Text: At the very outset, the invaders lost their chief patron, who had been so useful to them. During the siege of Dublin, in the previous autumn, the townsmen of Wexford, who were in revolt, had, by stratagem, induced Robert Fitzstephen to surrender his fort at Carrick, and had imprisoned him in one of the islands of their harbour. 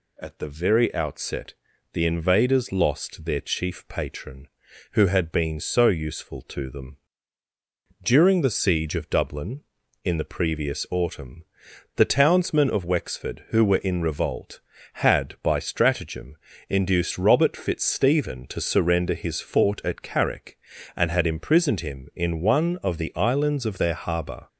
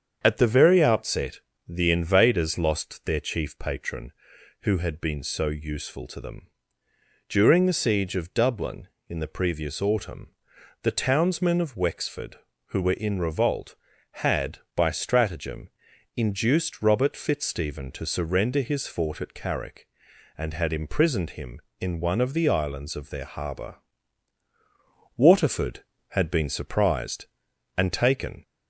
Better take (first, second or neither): first